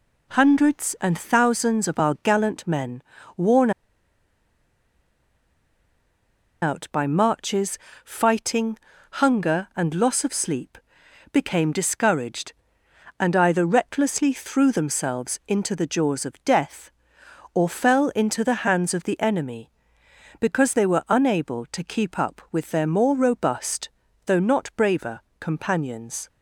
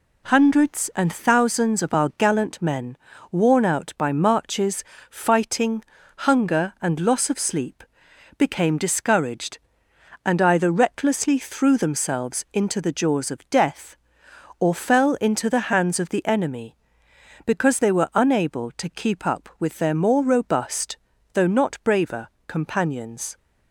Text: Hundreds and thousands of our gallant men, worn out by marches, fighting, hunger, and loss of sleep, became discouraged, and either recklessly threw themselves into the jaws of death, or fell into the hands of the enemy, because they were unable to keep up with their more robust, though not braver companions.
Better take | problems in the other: second | pauses between "worn" and "out"; strong; at 3.7 s; 2.9 s long // pauses between "braver" and "companions"; slight; at 25.1 s; 0.22 s long; slight in the second

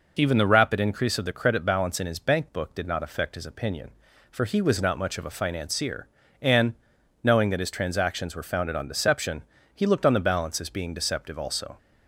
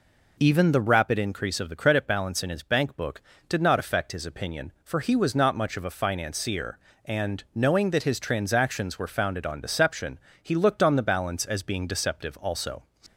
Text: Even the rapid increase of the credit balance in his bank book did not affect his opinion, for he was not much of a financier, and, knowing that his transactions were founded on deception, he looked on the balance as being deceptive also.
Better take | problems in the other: neither | none

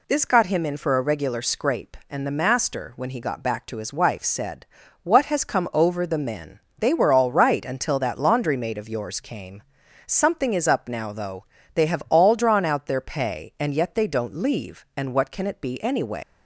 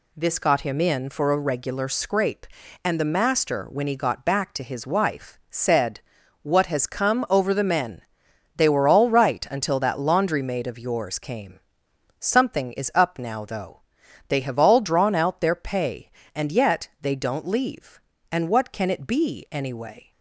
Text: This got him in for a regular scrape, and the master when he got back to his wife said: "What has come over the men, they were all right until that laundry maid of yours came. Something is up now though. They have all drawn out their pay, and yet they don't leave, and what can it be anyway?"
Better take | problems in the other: second | leaves "anyway" unfinished; at 16.2 s; 130 ms

